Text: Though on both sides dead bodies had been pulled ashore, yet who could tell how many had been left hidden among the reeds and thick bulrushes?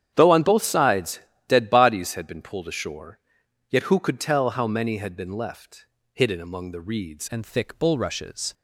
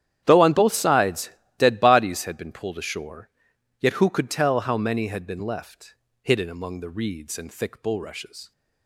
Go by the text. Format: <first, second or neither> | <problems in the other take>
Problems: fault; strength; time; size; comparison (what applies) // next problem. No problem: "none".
second | starts louder than the rest; strong; until 1.1 s; 9.5 dB; strong in the second // pauses between "sides" and "dead"; slight; at 1.2 s; 0.26 s long; slight in the second // pauses between "left" and "hidden"; slight; at 5.8 s; 0.26 s long; slight in the second // changes voice at "and"; from 7.2 s on; 1.3 s long